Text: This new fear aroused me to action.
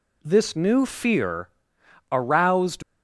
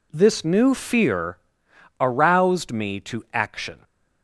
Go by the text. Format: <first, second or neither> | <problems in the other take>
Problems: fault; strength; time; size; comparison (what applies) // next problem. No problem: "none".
second | pauses between "fear" and "aroused"; noticeable; at 1.4 s; 0.64 s long; noticeable in the second // stops before "me to action"; at 2.8 s